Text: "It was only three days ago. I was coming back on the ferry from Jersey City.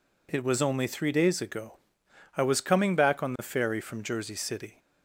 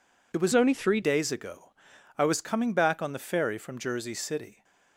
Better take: first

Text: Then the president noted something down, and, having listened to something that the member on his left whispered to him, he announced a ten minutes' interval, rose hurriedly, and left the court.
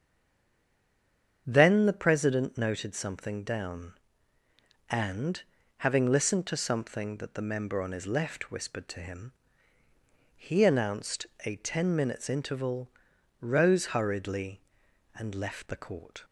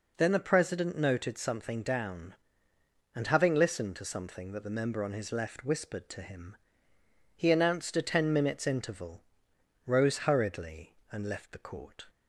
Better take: second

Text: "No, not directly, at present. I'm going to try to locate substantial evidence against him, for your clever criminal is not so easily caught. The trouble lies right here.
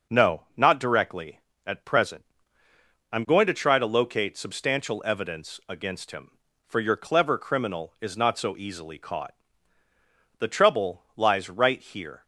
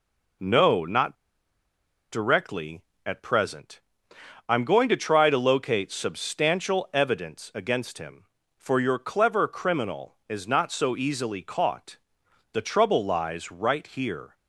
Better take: first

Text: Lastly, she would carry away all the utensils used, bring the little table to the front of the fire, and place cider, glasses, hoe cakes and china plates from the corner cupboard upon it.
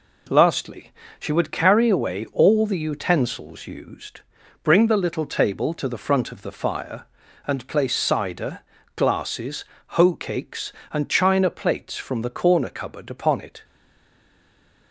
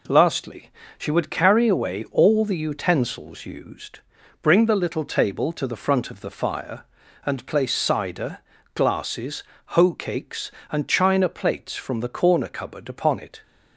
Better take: second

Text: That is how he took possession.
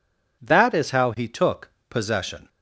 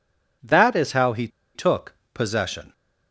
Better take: first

